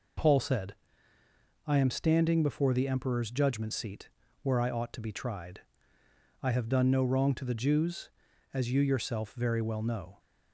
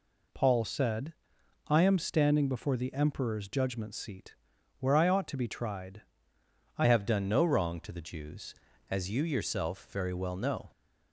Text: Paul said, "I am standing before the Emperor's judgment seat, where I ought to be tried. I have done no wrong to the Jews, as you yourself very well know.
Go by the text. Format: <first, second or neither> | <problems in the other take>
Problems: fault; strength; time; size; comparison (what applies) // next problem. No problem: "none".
first | changes voice at "have"; from 6.8 s on; 3.9 s long